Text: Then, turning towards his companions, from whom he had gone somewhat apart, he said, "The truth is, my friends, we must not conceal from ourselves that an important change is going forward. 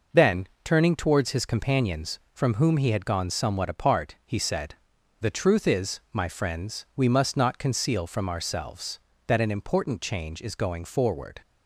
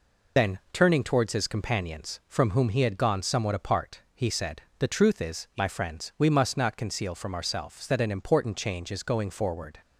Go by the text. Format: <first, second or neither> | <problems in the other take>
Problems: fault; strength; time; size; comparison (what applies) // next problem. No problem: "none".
first | loses the start of "Then"; at 0.3 s; 45 ms